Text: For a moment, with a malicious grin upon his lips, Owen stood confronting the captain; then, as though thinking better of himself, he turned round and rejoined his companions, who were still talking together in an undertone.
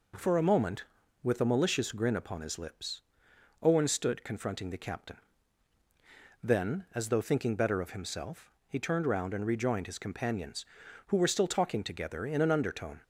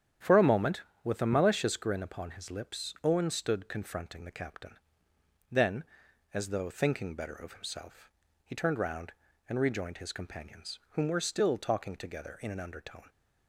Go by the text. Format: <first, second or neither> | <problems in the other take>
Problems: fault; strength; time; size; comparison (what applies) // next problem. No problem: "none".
first | starts louder than the rest; strong; until 1.4 s; 9 dB // says "whom" for "who"; at 10.8 s